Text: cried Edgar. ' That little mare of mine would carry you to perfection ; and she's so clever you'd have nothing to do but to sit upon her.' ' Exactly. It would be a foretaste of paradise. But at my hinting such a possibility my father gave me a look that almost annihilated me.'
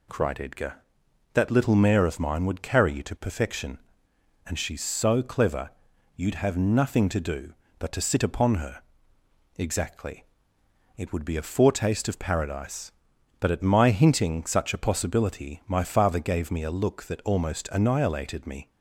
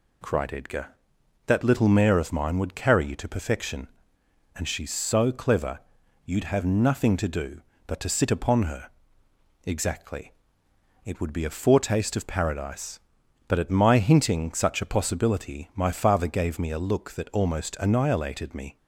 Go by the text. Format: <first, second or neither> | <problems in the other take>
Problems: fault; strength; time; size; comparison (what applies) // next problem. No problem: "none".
neither | pauses between "clever" and "you'd"; the same in both